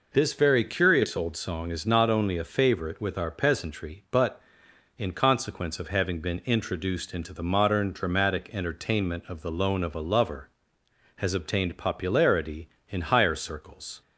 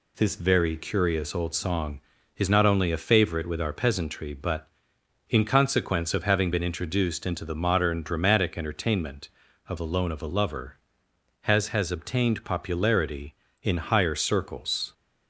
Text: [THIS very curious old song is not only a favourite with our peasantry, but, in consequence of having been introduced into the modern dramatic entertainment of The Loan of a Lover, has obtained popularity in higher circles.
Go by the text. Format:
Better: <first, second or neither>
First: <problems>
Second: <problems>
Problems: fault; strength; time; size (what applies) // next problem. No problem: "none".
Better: first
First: none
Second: says "has" twice; at 11.6 s